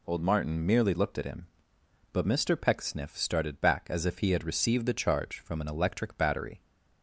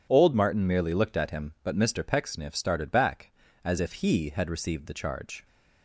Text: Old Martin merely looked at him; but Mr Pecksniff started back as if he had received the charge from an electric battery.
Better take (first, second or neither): first